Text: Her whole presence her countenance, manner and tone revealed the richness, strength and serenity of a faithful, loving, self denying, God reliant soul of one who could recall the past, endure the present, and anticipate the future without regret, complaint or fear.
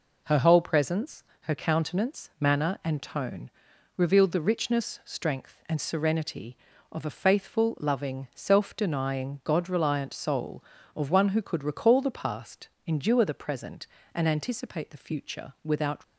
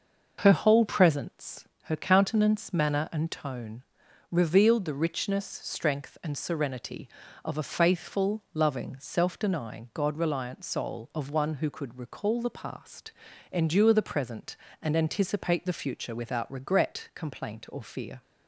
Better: second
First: pauses between "presence" and "her"; slight; at 1.2 s; 0.20 s long // pauses between "tone" and "revealed"; noticeable; at 3.5 s; 0.46 s long // stops before "regret complaint or fear"; at 16.0 s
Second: pauses between "presence" and "her"; slight; at 1.6 s; 0.16 s long // pauses between "tone" and "revealed"; noticeable; at 3.8 s; 0.48 s long

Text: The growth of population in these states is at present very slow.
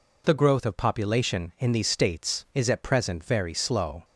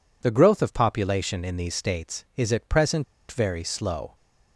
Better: first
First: none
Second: pauses between "present" and "very"; slight; at 3.0 s; 0.26 s long

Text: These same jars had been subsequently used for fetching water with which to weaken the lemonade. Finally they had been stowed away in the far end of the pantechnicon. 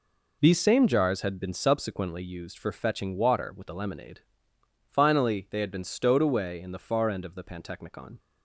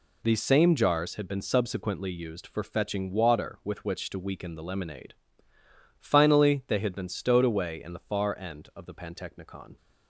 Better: second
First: skips "which to weaken"; at 3.6 s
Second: none

